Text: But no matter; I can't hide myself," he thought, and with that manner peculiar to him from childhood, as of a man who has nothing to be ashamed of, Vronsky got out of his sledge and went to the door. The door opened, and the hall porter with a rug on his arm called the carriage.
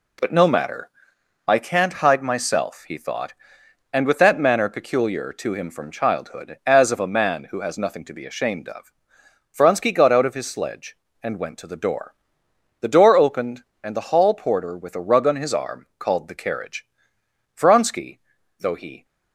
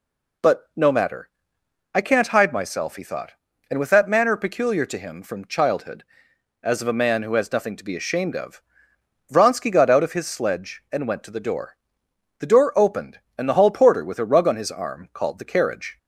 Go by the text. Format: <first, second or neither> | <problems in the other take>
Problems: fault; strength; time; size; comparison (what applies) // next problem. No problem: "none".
second | goes on to say "Vronsky though he"; from 17.5 s on; 1.5 s long